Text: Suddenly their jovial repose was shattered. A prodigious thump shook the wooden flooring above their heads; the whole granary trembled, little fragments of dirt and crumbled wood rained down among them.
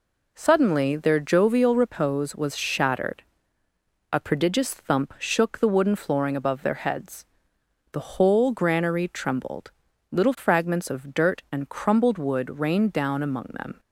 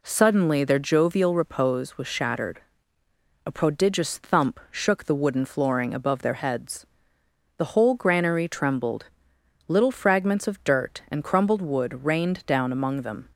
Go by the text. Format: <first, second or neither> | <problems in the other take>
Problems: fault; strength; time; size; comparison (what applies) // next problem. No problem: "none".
neither | none